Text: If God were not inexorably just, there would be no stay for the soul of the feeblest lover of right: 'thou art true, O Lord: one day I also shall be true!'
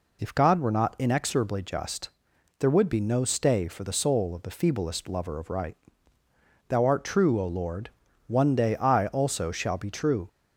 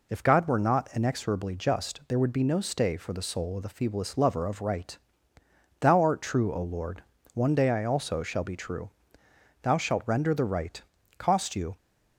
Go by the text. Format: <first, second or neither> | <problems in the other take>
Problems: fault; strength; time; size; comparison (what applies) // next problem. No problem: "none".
first | goes on to say "Thou shalt render the right cost you"; strong; from 9.6 s on; 2.1 s long